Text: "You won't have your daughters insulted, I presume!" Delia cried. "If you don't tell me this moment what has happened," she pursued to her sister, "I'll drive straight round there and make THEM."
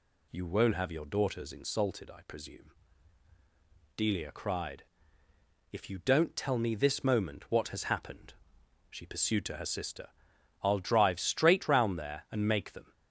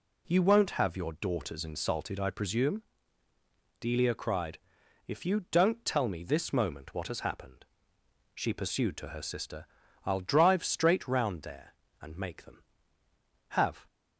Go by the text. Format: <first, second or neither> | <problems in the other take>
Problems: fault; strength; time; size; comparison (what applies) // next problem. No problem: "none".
first | goes on to say "HAVE"; slight; from 13.4 s on; 0.36 s long